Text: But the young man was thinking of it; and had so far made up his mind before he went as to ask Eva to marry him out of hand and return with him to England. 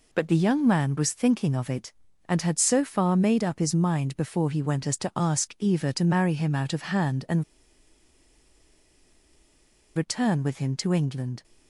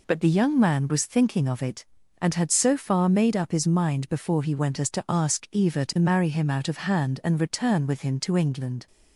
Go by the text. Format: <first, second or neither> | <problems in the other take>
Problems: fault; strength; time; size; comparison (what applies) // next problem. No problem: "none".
second | pauses between "and" and "return"; strong; at 7.4 s; 2.5 s long